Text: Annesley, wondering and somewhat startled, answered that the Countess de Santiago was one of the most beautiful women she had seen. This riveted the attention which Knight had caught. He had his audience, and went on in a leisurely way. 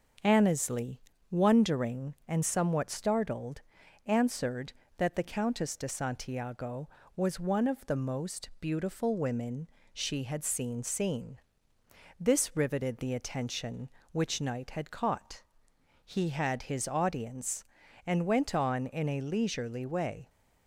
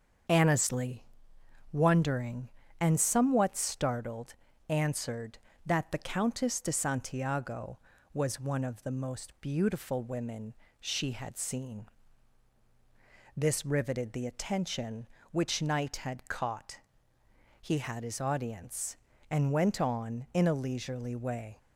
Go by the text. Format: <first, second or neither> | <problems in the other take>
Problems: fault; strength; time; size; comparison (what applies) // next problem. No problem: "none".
second | starts louder than the rest; until 1.5 s; 6.5 dB; strong in the second // pauses between "women" and "she"; slight; at 9.6 s; 0.26 s long; slight in the second // says "seen" twice; at 10.8 s